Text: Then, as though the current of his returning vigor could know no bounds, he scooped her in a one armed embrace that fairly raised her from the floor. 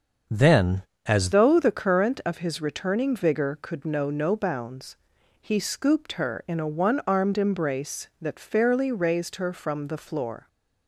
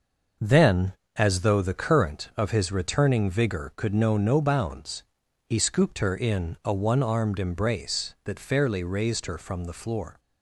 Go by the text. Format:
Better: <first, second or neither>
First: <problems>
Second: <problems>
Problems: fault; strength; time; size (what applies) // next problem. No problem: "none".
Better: second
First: starts louder than the rest; until 1.5 s; 7 dB // changes voice at "though"; from 1.3 s on; 9.1 s long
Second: none